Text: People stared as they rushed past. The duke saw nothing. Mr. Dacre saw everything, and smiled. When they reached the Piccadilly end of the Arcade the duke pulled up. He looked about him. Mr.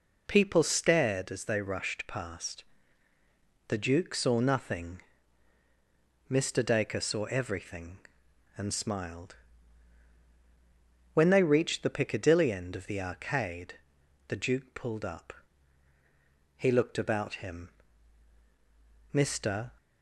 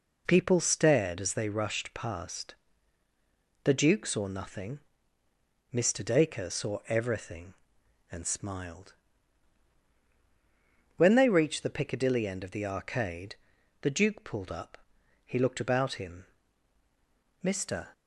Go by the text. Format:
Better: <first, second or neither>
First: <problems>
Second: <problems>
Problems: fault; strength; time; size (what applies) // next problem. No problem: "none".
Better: neither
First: pauses between "Arcade" and "the"; noticeable; at 13.7 s; 0.54 s long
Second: pauses between "Arcade" and "the"; noticeable; at 13.3 s; 0.46 s long